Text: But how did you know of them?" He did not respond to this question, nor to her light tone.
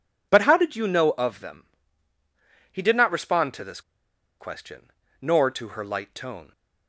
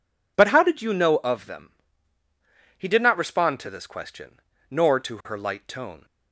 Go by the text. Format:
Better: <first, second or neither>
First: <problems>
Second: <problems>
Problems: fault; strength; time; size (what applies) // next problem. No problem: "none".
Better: second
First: pauses between "this" and "question"; noticeable; at 3.8 s; 0.59 s long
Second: none